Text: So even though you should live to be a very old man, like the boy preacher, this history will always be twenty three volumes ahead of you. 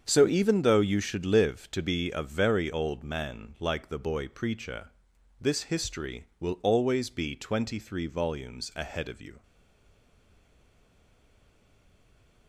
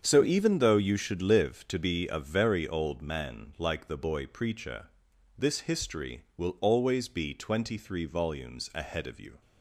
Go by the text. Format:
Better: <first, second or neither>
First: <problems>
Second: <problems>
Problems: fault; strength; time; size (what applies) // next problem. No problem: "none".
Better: second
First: starts louder than the rest; strong; until 1.0 s; 7.5 dB // stays silent after the last word; strong; from 9.4 s on; 3.0 s long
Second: starts louder than the rest; strong; until 1.0 s; 7.5 dB